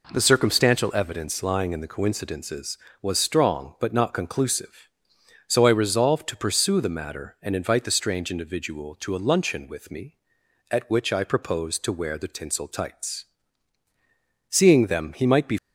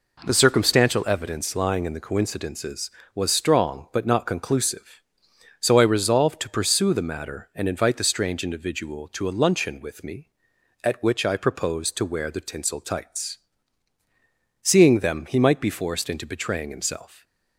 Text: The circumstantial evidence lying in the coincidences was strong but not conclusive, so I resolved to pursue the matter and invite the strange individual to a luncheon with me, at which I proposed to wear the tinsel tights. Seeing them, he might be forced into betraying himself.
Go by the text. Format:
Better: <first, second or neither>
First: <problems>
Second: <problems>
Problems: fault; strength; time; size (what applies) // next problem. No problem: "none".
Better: second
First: stops before "forced into betraying himself"; at 15.5 s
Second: none